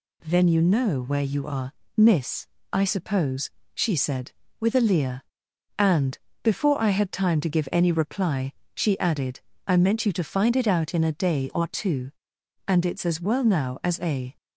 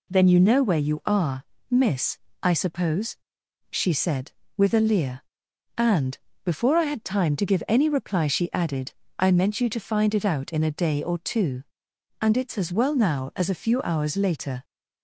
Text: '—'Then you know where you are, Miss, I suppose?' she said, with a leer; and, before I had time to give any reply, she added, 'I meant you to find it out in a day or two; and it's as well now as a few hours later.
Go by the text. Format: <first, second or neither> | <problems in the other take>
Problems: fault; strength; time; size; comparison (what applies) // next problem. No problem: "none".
second | stops before "few hours later"; at 14.3 s